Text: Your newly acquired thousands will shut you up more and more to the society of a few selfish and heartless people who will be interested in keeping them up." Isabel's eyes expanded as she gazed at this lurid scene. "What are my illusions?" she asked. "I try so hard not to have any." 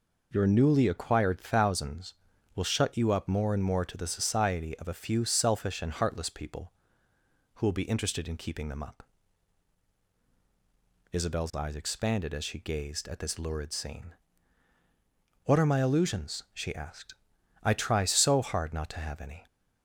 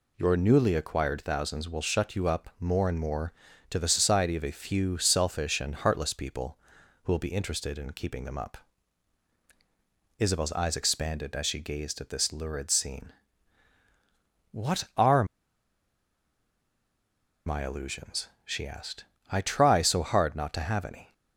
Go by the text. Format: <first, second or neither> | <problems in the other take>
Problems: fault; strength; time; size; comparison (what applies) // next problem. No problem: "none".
first | pauses between "are" and "my"; strong; at 15.2 s; 2.2 s long